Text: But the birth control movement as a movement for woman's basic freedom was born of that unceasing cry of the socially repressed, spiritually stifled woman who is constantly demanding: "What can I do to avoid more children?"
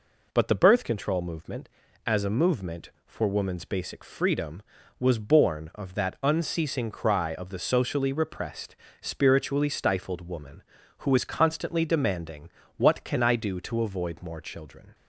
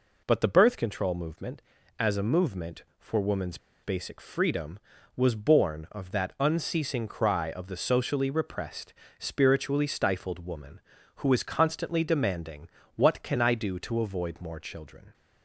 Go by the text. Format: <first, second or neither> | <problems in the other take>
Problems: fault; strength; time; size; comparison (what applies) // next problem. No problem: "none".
first | pauses between "woman's" and "basic"; slight; at 3.5 s; 0.26 s long